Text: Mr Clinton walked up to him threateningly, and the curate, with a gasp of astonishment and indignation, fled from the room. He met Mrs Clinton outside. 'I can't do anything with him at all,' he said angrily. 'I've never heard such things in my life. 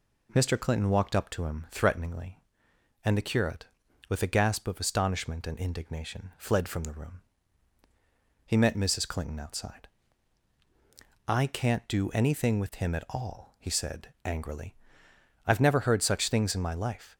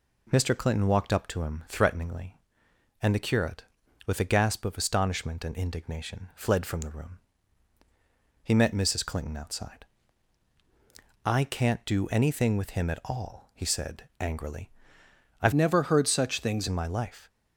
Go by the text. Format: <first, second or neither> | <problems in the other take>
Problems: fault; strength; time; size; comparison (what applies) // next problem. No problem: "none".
first | changes voice from "never" to "things"; from 15.5 to 16.6 s; 1.1 s long